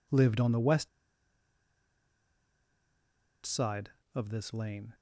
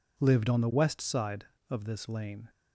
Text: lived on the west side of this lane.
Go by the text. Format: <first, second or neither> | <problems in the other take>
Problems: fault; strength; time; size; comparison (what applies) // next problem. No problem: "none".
second | pauses between "west" and "side"; strong; at 0.8 s; 2.5 s long